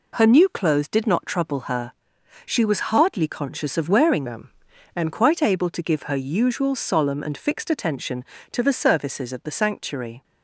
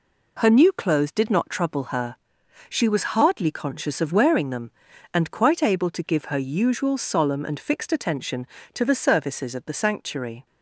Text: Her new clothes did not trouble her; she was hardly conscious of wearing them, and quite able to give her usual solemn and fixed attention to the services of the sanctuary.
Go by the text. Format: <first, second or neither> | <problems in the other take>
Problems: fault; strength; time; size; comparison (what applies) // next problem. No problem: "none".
second | changes voice from "them" to "and"; from 4.2 to 5.1 s; 0.9 s long